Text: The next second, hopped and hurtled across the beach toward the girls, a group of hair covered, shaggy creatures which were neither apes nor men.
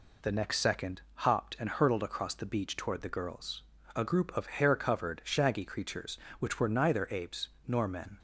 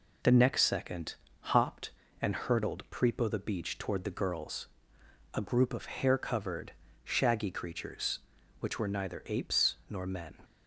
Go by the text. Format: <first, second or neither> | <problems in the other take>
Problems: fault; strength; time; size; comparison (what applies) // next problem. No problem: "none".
first | says "prepo" for "across"; at 2.9 s // pauses between "apes" and "nor"; slight; at 9.7 s; 0.16 s long; slight in the first